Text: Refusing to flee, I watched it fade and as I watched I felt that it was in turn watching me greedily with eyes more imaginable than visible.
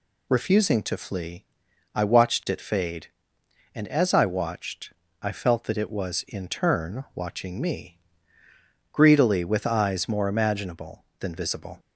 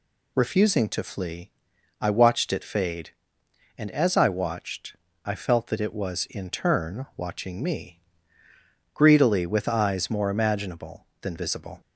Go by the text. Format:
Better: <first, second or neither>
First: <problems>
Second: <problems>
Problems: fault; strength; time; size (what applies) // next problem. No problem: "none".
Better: neither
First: pauses between "watched" and "I"; slight; at 4.9 s; 0.30 s long // pauses between "me" and "greedily"; noticeable; at 7.9 s; 0.94 s long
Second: pauses between "watched" and "I"; slight; at 4.9 s; 0.30 s long // pauses between "me" and "greedily"; noticeable; at 7.9 s; 0.94 s long